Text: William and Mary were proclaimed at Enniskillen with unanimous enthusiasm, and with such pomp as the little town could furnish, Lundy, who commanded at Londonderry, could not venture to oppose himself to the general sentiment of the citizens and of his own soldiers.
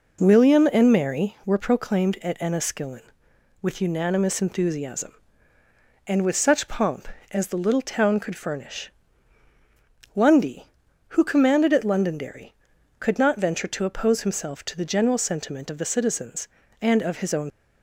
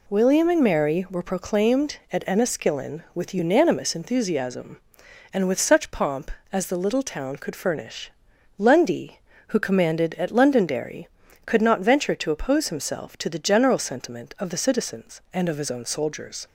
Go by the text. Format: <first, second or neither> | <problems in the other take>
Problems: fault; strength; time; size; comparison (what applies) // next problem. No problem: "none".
second | stops before "soldiers"; at 17.5 s